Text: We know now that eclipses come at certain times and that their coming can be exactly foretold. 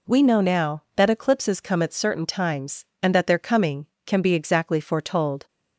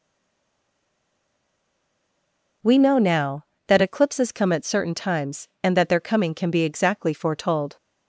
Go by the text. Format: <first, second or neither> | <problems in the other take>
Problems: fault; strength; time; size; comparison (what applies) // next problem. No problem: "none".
first | stays silent before the first word; strong; until 2.6 s; 2.6 s long